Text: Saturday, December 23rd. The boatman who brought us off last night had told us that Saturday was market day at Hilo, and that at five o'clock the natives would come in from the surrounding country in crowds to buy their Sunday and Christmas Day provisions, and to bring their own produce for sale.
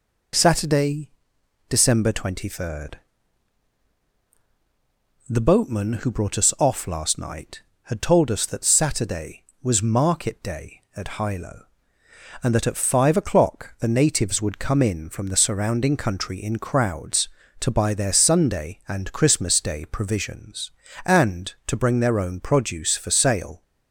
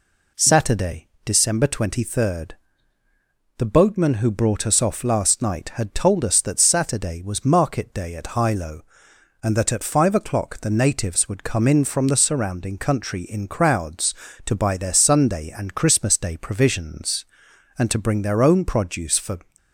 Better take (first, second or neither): first